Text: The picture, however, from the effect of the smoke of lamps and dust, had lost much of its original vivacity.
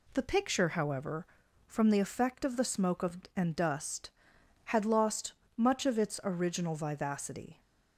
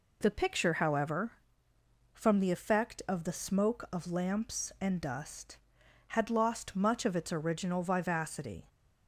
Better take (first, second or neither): second